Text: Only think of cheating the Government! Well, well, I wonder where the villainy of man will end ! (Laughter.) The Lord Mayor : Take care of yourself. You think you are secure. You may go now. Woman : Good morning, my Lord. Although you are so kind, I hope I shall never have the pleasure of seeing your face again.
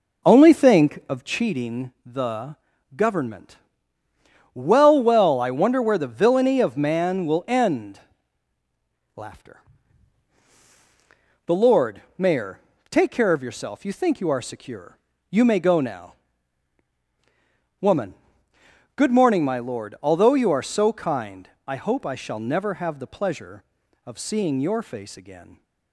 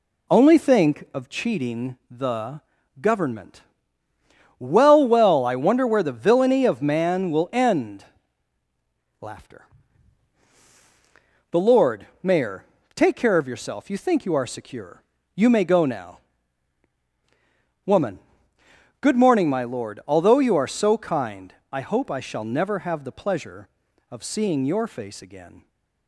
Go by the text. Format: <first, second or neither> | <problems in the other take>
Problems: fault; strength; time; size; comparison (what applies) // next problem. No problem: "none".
second | starts louder than the rest; noticeable; until 1.5 s; 4 dB // pauses between "the" and "Government"; at 2.5 s; 0.40 s long; also in the second // pauses between "Lord" and "Mayor"; slight; at 12.0 s; 0.16 s long; slight in the second